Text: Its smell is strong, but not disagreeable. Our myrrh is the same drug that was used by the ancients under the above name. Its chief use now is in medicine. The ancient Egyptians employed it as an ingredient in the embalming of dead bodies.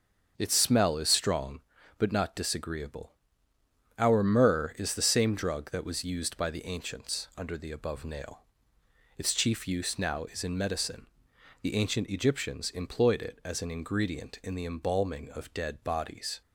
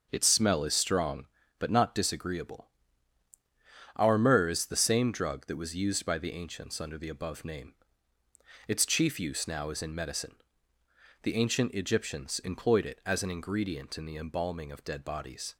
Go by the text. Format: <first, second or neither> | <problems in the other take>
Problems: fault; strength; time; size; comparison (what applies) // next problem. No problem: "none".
second | starts louder than the rest; until 1.3 s; 7 dB; also in the second // says "nail" for "name"; at 8.0 s